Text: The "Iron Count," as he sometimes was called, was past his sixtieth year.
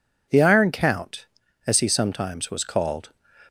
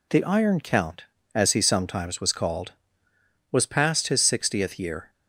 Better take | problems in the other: second | stops before "was past his sixtieth year"; at 3.4 s

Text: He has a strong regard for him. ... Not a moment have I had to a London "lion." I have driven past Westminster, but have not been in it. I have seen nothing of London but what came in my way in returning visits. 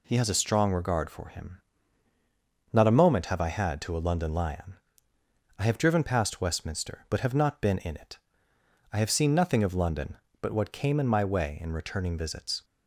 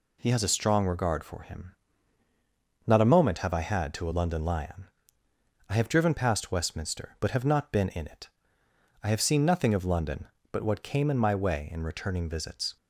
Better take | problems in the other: neither | none

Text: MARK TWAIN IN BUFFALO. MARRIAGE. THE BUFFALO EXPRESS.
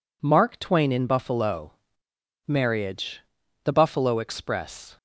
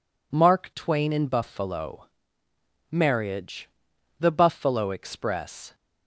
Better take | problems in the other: neither | none

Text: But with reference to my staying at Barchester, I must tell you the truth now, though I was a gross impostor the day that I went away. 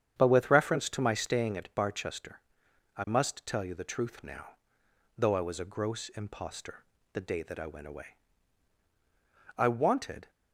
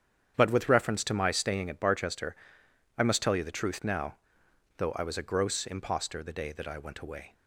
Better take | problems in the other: second | starts louder than the rest; strong; until 1.1 s; 8.5 dB; strong in the second // pauses between "impostor" and "the"; slight; at 6.8 s; 0.30 s long // goes on to say "I wanted"; noticeable; from 9.5 s on; 0.72 s long

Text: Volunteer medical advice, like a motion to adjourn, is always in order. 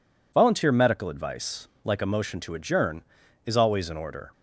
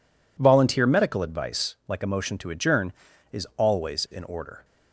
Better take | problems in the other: neither | none

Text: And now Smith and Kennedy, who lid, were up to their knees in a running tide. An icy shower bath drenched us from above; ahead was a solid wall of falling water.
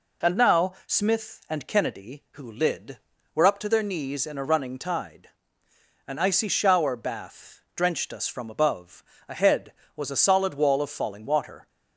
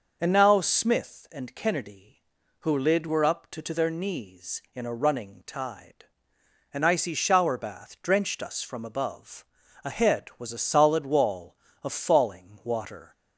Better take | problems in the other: first | says "to" twice; at 3.6 s

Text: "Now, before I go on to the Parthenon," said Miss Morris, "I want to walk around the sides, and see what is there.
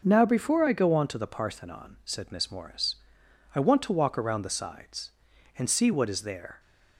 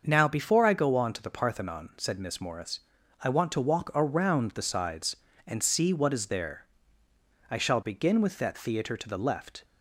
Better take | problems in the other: first | starts louder than the rest; until 1.0 s; 6.5 dB; noticeable in the first // goes on to say "I shall begin with that theatre to the left"; strong; from 7.5 s on; 2.1 s long

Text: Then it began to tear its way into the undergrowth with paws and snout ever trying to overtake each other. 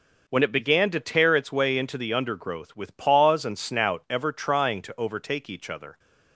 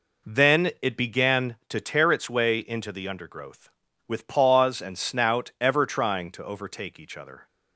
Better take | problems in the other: second | says "When" for "Then"; at 0.2 s

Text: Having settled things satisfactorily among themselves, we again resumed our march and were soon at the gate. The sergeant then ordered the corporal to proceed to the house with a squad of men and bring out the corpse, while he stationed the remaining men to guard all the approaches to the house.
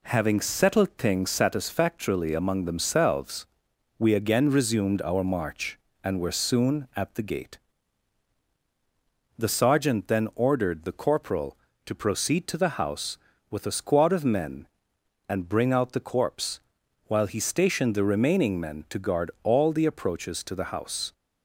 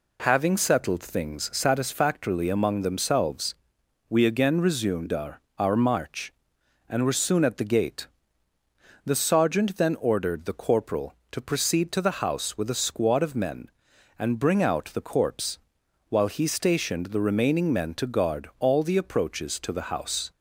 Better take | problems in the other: first | says "our" twice; at 5.5 s

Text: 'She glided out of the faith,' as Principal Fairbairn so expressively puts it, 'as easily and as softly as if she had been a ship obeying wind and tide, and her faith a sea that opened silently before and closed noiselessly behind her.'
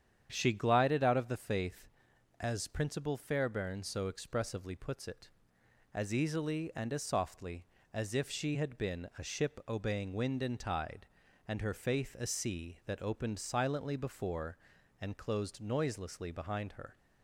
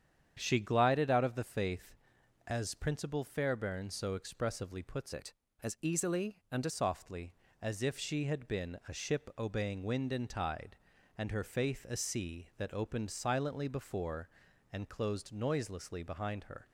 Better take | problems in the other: first | starts louder than the rest; strong; until 1.3 s; 8.5 dB; strong in the first // changes voice from "it" to "as"; from 5.1 to 6.7 s; 1.6 s long

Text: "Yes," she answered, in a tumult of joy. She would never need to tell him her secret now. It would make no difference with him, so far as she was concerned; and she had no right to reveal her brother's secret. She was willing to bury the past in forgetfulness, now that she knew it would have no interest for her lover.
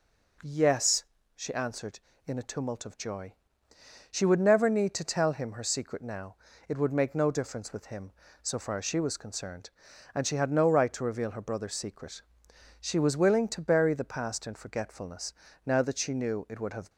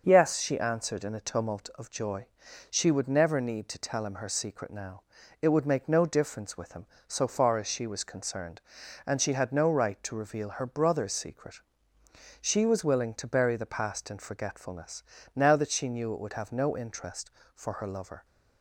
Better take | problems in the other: second | stops before "no interest for her lover"; at 16.8 s

